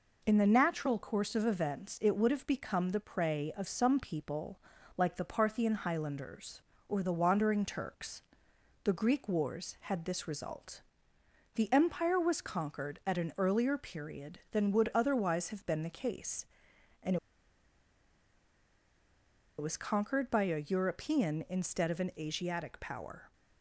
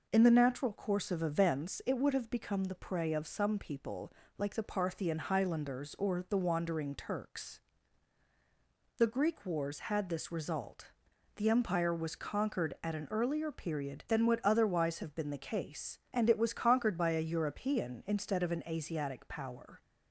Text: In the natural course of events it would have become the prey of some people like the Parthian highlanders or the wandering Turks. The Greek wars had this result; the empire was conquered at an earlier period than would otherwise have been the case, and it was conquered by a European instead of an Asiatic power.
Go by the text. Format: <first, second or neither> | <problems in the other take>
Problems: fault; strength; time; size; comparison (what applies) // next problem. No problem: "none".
second | pauses between "people" and "like"; slight; at 4.6 s; 0.36 s long; slight in the second // pauses between "and" and "it"; strong; at 17.1 s; 2.4 s long